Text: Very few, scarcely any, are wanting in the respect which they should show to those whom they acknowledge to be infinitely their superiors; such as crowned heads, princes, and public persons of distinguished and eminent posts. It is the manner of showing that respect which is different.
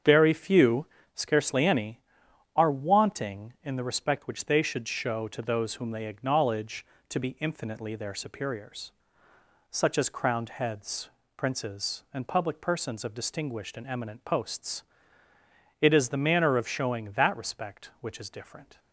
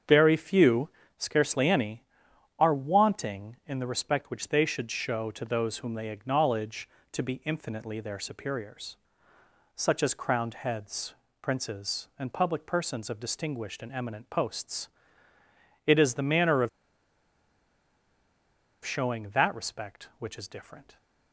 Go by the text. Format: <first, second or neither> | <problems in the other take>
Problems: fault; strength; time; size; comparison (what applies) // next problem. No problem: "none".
first | starts louder than the rest; strong; until 1.3 s; 7.5 dB; strong in the first // pauses between "of" and "showing"; strong; at 16.6 s; 2.1 s long